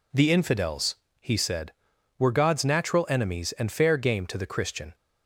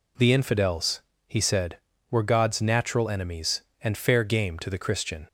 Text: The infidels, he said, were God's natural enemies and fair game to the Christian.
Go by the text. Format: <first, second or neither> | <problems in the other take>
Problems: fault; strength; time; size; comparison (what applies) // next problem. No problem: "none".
neither | none